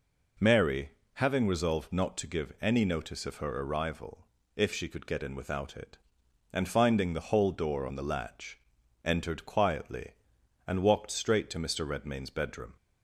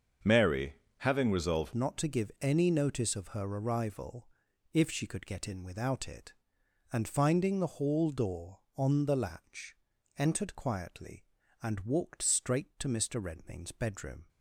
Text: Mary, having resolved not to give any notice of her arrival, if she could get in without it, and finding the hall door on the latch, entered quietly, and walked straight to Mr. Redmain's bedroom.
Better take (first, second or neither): first